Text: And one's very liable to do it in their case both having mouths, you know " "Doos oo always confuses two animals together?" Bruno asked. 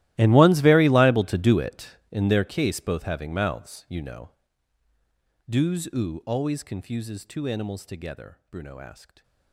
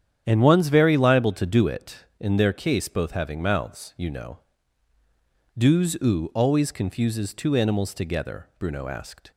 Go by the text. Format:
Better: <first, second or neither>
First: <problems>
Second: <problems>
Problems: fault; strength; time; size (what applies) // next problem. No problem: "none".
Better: second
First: gets quieter; strong; throughout; 21 dB // starts louder than the rest; strong; until 1.1 s; 16 dB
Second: starts louder than the rest; strong; until 1.2 s; 9.5 dB